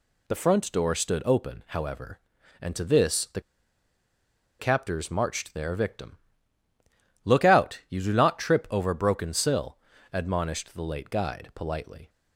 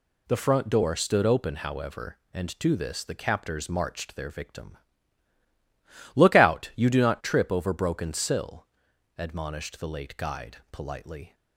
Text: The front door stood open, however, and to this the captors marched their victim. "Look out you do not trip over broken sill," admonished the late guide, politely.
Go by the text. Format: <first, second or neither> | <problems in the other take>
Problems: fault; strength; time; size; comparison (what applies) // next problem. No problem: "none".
second | pauses between "the" and "captors"; at 3.4 s; 1.1 s long